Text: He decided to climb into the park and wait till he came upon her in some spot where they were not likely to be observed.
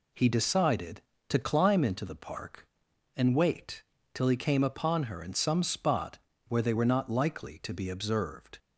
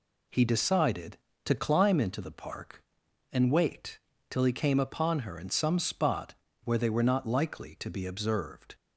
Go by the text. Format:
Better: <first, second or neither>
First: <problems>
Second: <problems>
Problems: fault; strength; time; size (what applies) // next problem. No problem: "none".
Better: neither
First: pauses between "wait" and "till"; slight; at 3.8 s; 0.32 s long // pauses between "spot" and "where"; slight; at 6.1 s; 0.30 s long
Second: pauses between "wait" and "till"; slight; at 3.9 s; 0.32 s long // pauses between "spot" and "where"; slight; at 6.3 s; 0.30 s long